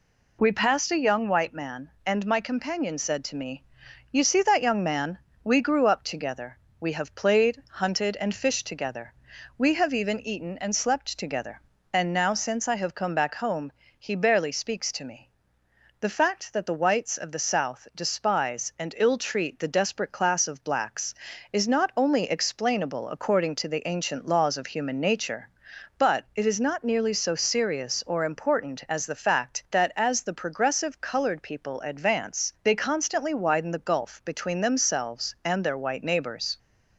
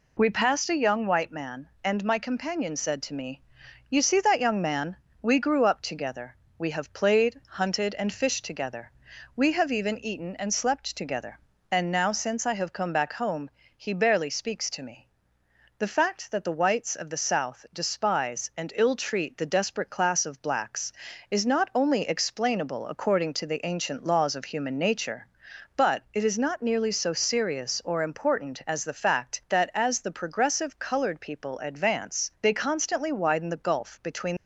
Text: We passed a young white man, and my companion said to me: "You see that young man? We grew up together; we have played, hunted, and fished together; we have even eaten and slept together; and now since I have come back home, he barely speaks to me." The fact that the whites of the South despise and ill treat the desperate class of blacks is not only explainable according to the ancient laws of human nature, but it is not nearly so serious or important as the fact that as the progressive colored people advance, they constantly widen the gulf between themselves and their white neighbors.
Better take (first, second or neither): first